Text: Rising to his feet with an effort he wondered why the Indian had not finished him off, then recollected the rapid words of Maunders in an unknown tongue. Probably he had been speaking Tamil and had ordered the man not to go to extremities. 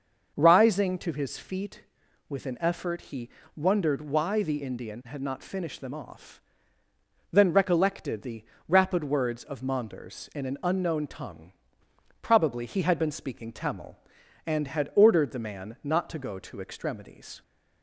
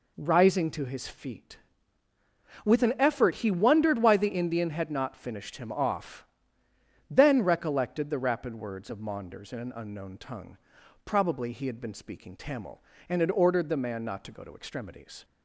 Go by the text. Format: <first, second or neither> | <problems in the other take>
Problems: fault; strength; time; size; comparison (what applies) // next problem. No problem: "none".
second | starts louder than the rest; until 1.3 s; 6 dB // pauses between "he" and "wondered"; slight; at 3.2 s; 0.26 s long // says "them" for "him"; at 5.7 s // pauses between "the" and "rapid"; slight; at 8.4 s; 0.24 s long